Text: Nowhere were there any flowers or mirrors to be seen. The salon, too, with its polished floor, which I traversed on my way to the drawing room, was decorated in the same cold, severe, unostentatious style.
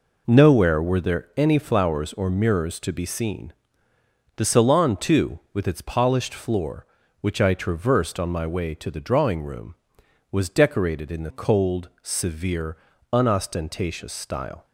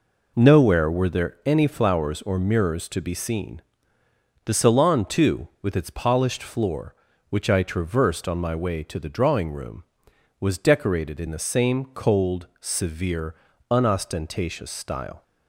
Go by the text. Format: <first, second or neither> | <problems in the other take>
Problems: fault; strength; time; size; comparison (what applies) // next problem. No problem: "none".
second | skips "same"; at 11.3 s